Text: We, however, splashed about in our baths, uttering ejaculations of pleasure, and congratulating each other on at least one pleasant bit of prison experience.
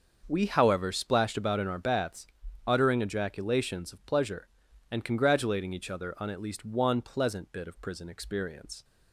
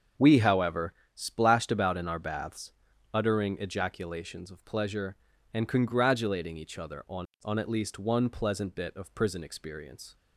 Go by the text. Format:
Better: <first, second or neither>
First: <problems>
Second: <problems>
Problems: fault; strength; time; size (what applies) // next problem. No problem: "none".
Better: first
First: starts louder than the rest; until 1.2 s; 6.5 dB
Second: starts louder than the rest; until 1.4 s; 6.5 dB // says "on" twice; at 7.4 s